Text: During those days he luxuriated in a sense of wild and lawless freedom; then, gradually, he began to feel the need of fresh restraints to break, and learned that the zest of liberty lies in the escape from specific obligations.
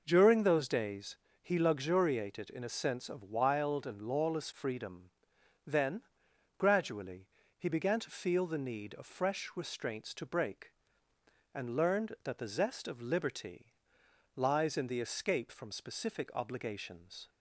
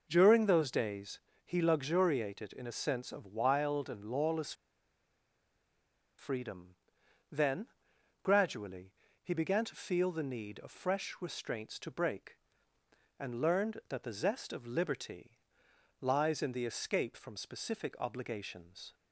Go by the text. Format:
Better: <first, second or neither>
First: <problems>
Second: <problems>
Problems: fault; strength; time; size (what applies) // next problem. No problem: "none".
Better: first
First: pauses between "days" and "he"; slight; at 1.1 s; 0.24 s long // pauses between "liberty" and "lies"; noticeable; at 13.7 s; 0.64 s long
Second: pauses between "days" and "he"; slight; at 1.1 s; 0.24 s long // pauses between "lawless" and "freedom"; strong; at 4.5 s; 1.6 s long // pauses between "liberty" and "lies"; noticeable; at 15.3 s; 0.64 s long